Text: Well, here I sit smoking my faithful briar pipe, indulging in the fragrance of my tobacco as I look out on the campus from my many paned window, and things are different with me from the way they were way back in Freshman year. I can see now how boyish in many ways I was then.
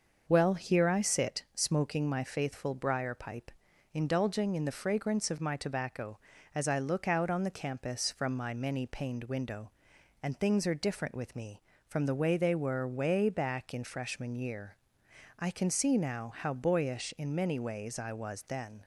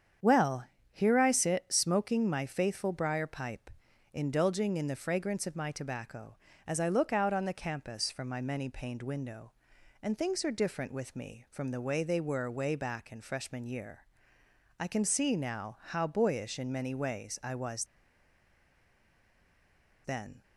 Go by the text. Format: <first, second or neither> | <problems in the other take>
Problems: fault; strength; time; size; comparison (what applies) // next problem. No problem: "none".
first | starts louder than the rest; strong; until 1.4 s; 8 dB; noticeable in the first // pauses between "was" and "then"; strong; at 17.8 s; 2.1 s long